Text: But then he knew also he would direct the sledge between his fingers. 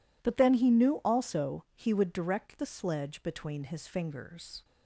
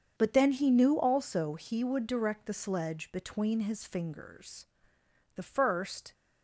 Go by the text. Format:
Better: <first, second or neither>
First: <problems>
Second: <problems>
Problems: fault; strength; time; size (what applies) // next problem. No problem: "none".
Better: first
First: none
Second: starts louder than the rest; strong; until 1.1 s; 7 dB // goes on to say "The first"; noticeable; from 5.3 s on; 0.78 s long